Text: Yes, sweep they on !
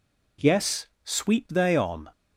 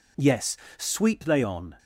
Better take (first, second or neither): neither